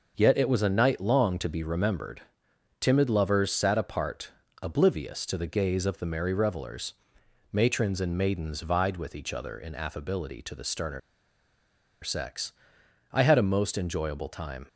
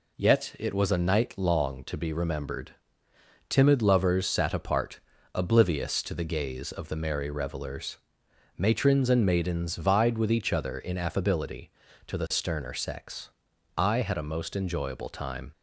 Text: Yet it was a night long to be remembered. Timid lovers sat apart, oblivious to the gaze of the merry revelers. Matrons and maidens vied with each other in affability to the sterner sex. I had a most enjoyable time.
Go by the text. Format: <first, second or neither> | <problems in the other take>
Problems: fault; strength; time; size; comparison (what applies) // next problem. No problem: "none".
second | pauses between "sterner" and "sex"; at 10.9 s; 1.0 s long